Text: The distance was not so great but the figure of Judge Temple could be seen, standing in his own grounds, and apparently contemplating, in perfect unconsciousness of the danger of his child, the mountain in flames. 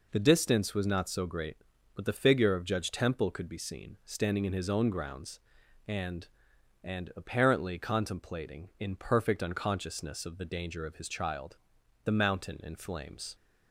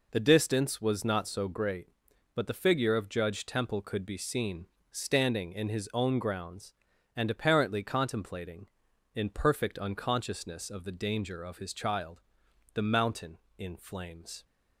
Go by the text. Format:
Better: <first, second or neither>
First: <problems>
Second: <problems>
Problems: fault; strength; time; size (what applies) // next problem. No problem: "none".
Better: second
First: says "and" twice; at 6.8 s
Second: none